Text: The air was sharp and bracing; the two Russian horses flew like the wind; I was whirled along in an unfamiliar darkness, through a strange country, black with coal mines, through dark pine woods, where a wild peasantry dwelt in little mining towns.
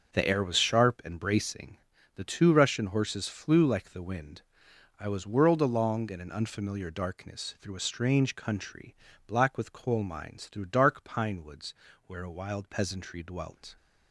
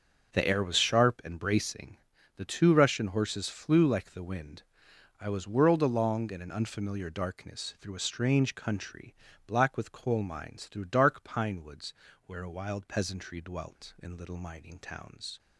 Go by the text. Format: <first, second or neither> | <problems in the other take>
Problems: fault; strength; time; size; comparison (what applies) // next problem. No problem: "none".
second | stops before "in little mining towns"; at 13.7 s